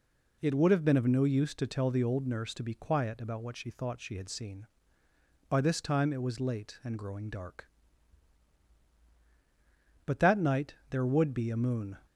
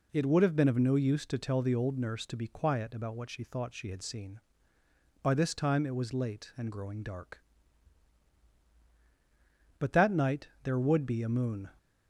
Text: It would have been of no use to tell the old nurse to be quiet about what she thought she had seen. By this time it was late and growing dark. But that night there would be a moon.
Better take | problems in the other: neither | pauses between "night" and "there"; slight; the same in both

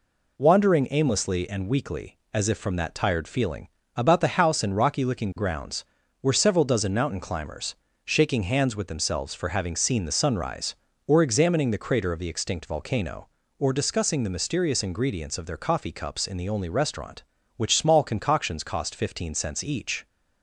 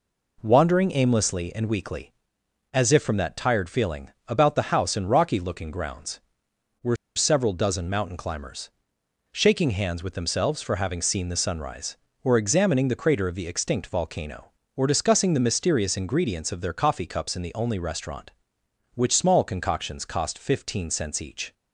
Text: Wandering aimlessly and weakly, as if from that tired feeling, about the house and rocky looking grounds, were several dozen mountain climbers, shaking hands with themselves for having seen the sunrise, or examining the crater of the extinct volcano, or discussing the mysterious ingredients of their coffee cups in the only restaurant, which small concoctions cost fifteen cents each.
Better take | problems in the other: first | pauses between "were" and "several"; slight; at 6.9 s; 0.20 s long

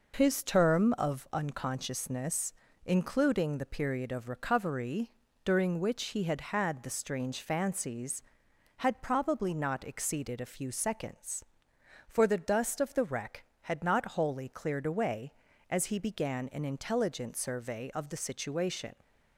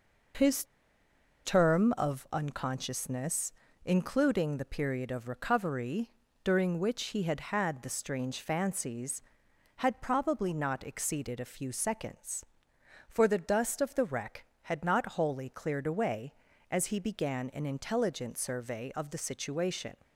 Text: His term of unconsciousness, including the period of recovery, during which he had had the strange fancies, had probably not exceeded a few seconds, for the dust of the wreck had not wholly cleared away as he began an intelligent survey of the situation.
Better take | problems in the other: first | pauses between "His" and "term"; noticeable; at 0.6 s; 0.80 s long

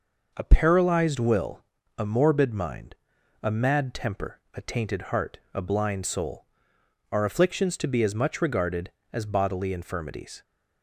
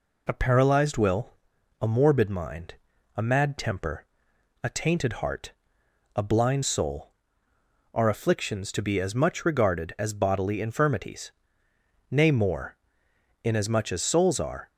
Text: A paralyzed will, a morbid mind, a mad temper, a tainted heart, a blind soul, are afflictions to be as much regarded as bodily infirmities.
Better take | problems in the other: first | goes on to say "Nay more inasmuch as souls are"; strong; from 12.1 s on; 2.6 s long

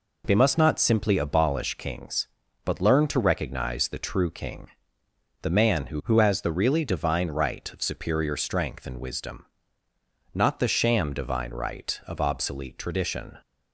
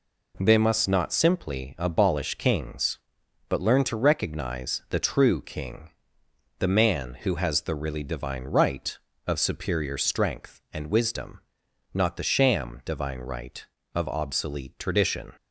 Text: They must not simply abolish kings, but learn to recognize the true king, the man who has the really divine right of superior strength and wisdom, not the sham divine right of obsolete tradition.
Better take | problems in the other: second | says "who" twice; at 6.0 s

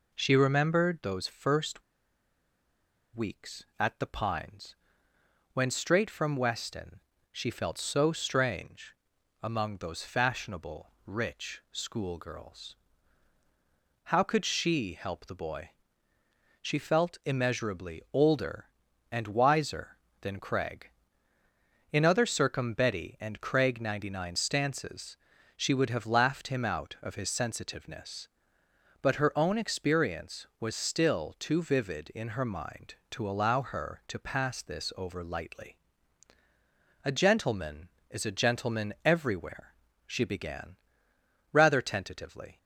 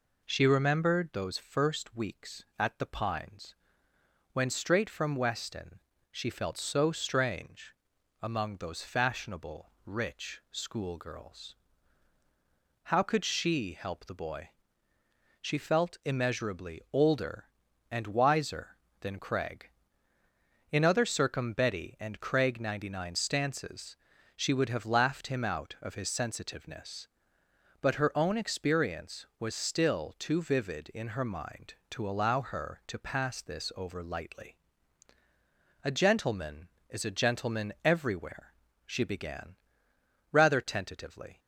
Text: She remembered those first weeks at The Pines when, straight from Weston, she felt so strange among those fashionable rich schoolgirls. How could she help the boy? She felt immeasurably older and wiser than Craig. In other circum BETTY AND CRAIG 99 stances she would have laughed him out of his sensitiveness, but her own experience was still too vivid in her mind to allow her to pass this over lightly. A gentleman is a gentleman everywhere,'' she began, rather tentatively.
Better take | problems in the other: second | pauses between "first" and "weeks"; strong; at 1.8 s; 1.3 s long // pauses between "Pines" and "when"; noticeable; at 4.7 s; 0.78 s long; noticeable in the second // pauses between "strange" and "among"; noticeable; at 8.9 s; 0.46 s long; noticeable in the second // pauses between "stances" and "she"; at 25.1 s; 0.40 s long; also in the second

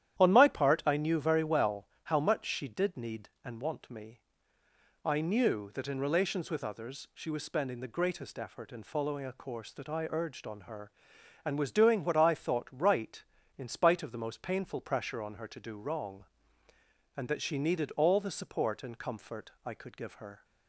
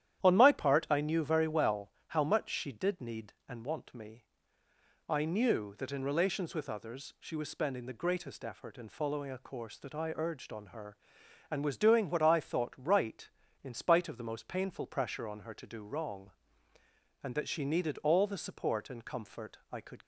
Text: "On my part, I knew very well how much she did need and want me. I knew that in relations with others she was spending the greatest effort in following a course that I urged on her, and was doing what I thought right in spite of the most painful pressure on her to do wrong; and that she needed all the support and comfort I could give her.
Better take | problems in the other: first | starts louder than the rest; strong; until 1.2 s; 11 dB; strong in the first // pauses between "well" and "how"; slight; at 1.9 s; 0.16 s long; slight in the first // pauses between "comfort" and "I"; slight; at 19.5 s; 0.16 s long; slight in the first // stops before "give her"; at 20.0 s

